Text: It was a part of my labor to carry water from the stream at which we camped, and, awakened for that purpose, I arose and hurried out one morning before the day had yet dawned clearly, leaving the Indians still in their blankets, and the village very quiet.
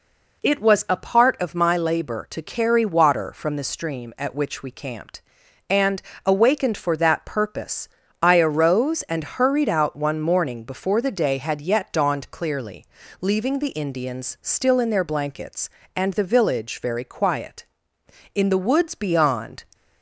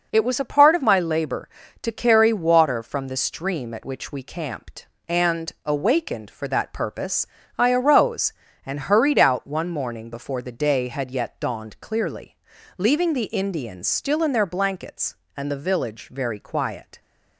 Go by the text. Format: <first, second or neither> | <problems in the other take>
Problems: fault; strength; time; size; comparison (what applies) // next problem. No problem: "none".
second | goes on to say "In the woods beyond"; noticeable; from 18.3 s on; 1.2 s long